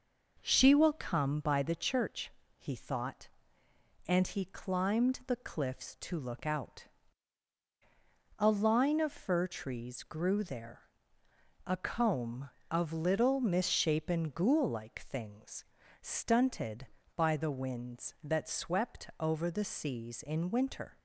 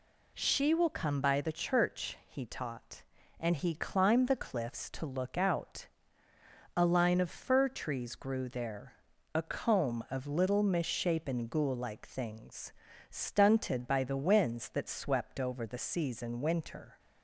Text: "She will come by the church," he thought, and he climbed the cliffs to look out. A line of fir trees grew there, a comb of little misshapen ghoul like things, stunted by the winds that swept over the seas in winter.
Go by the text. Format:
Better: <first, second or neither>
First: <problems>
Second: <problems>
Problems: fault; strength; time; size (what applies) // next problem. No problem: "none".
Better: first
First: none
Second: says "taught" for "thought"; at 2.4 s